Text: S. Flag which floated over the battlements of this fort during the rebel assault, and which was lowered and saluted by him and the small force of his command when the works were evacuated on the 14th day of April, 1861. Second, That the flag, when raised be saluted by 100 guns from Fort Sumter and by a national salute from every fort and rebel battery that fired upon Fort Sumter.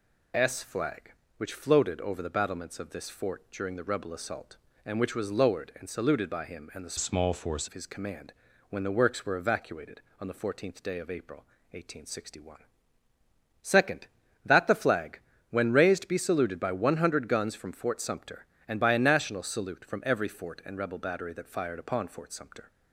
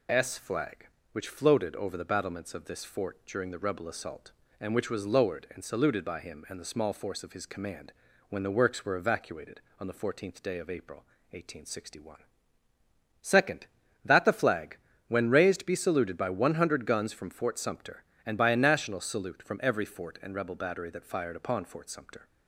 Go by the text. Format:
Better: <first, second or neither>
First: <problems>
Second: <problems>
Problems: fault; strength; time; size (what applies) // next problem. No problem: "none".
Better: second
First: changes voice from "small" to "force"; from 6.9 to 7.6 s; 0.7 s long // pauses between "command" and "when"; slight; at 8.3 s; 0.36 s long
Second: pauses between "command" and "when"; slight; at 7.9 s; 0.36 s long